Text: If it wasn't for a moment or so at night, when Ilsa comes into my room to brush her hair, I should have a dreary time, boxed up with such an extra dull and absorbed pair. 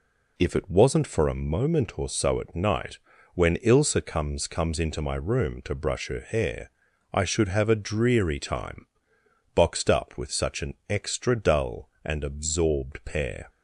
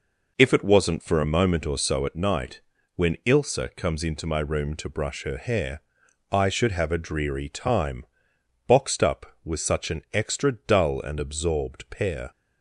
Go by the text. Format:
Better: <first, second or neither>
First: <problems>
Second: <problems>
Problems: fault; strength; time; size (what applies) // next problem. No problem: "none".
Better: second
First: says "comes" twice; at 4.4 s // pauses between "an" and "extra"; slight; at 10.7 s; 0.16 s long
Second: none